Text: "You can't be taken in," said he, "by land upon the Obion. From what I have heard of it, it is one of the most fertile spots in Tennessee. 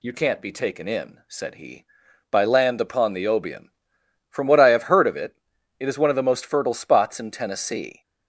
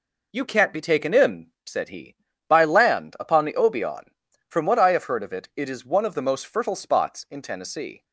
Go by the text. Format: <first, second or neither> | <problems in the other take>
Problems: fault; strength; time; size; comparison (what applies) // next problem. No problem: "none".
neither | none